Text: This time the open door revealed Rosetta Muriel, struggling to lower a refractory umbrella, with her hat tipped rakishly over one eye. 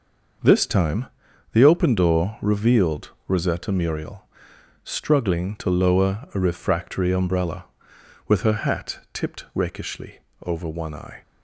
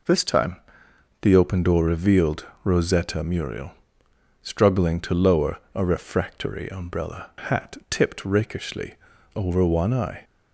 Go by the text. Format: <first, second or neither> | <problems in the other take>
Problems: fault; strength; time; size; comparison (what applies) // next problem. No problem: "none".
first | pauses between "time" and "the"; noticeable; at 0.5 s; 0.66 s long; also in the first // pauses between "revealed" and "Rosetta"; slight; at 2.4 s; 0.22 s long; slight in the first // pauses between "lower" and "a"; slight; at 5.5 s; 0.16 s long // skips "with her"; at 7.3 s // pauses between "rakishly" and "over"; at 8.9 s; 0.42 s long; slight in the first